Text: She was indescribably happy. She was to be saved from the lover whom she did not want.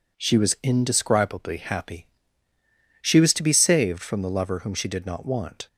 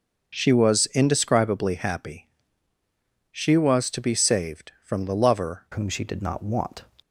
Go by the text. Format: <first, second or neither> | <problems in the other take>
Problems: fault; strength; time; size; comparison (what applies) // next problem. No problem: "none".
first | starts louder than the rest; until 1.4 s; 6.5 dB // changes voice at "whom"; from 5.7 s on; 1.1 s long